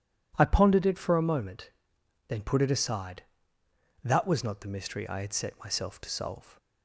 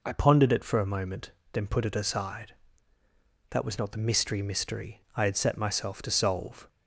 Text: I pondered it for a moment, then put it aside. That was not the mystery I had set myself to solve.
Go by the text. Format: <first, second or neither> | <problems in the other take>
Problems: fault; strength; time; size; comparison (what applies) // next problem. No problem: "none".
first | says "mystery" twice; at 4.4 s